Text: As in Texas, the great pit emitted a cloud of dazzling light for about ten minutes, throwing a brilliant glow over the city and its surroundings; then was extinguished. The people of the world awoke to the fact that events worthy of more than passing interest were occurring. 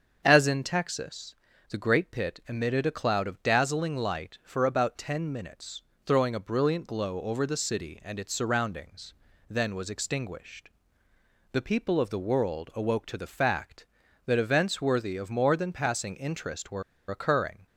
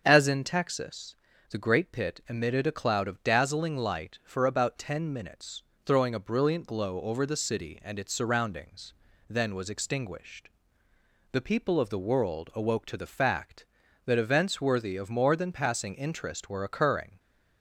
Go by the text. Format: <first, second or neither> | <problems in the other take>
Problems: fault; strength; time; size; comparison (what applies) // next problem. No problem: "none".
second | starts louder than the rest; strong; until 1.2 s; 7 dB; also in the second // pauses between "were" and "occurring"; slight; at 16.8 s; 0.27 s long